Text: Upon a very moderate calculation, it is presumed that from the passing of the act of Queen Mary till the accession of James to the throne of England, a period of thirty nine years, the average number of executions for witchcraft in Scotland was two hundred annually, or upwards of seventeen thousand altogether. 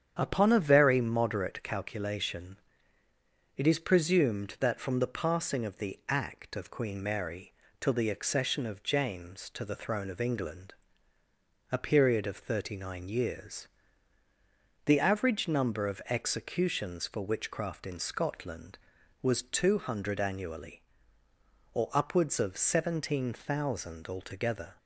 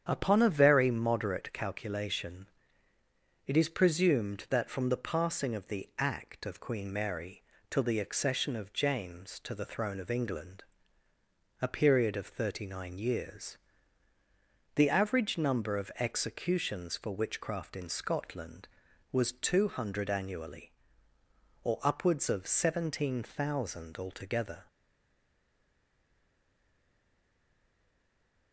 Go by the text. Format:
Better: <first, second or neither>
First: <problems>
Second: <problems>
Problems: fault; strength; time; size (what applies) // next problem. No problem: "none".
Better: first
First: starts louder than the rest; strong; until 1.2 s; 8.5 dB // pauses between "Mary" and "till"; slight; at 7.5 s; 0.26 s long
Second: starts louder than the rest; strong; until 1.0 s; 8 dB // pauses between "Mary" and "till"; slight; at 7.4 s; 0.26 s long // stays silent after the last word; strong; from 24.6 s on; 3.9 s long